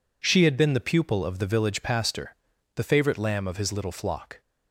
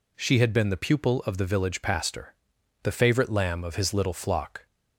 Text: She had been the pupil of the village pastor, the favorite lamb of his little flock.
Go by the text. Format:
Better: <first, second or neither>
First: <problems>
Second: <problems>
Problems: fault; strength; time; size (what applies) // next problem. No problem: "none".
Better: neither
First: none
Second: none